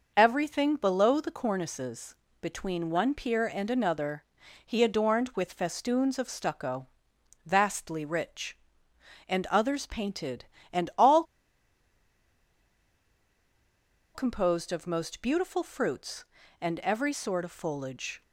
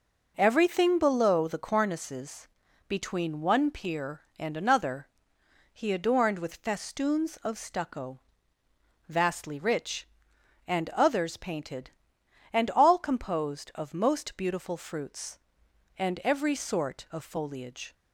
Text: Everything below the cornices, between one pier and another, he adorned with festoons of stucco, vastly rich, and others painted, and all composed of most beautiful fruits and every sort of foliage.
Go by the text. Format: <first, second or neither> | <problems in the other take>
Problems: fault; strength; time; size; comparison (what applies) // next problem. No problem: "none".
second | pauses between "all" and "composed"; strong; at 11.2 s; 2.9 s long